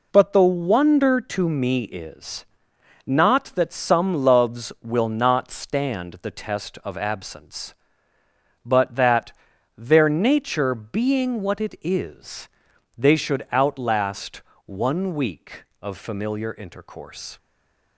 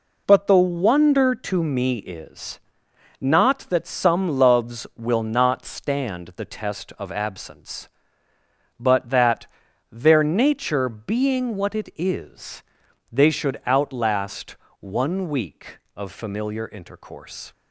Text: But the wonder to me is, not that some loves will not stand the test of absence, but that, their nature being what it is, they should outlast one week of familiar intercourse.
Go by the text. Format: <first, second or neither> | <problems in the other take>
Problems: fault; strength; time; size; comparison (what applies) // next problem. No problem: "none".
second | pauses between "outlast" and "one"; slight; at 14.4 s; 0.24 s long; slight in the second // stays silent after the last word; slight; from 17.3 s on; 0.6 s long